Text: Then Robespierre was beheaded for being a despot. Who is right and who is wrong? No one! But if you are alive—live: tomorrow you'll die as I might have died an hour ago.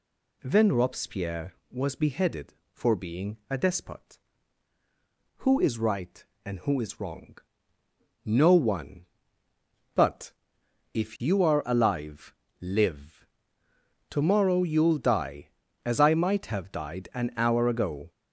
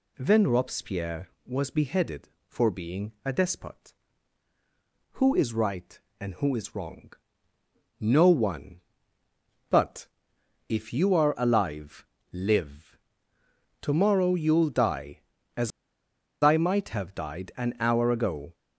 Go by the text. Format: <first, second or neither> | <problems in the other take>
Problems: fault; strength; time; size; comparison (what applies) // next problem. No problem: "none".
first | pauses between "But" and "if"; noticeable; at 10.0 s; 0.62 s long; noticeable in the first // pauses between "as" and "I"; noticeable; at 15.7 s; 0.73 s long